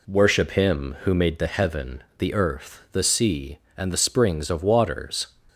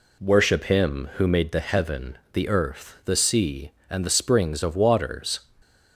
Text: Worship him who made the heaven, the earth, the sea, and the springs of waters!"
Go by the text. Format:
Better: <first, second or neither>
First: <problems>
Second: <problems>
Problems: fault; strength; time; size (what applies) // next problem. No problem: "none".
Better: neither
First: none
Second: none